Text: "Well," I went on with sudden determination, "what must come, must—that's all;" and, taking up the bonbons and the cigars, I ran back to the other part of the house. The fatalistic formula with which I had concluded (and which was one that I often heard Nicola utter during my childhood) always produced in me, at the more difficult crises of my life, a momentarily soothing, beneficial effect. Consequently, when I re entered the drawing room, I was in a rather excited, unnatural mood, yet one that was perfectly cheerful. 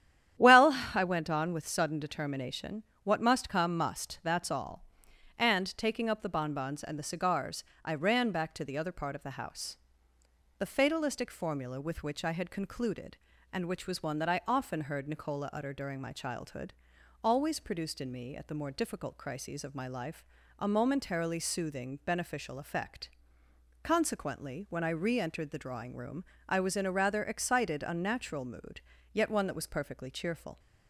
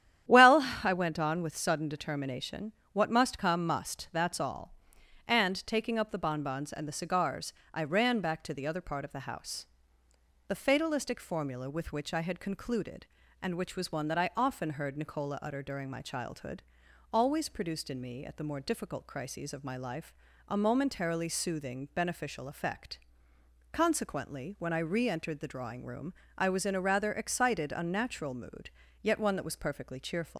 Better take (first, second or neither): first